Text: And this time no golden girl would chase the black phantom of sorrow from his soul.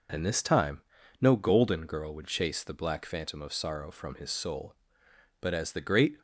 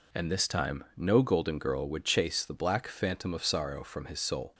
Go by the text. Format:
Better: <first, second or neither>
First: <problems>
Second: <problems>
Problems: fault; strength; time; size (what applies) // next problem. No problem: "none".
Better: second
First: pauses between "time" and "no"; at 0.8 s; 0.40 s long // goes on to say "But as the great"; noticeable; from 5.3 s on; 0.82 s long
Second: none